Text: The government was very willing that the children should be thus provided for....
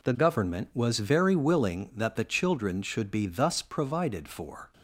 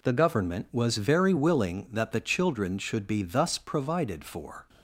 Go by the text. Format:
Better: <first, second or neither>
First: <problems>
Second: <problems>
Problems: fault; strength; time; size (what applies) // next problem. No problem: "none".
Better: neither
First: none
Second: none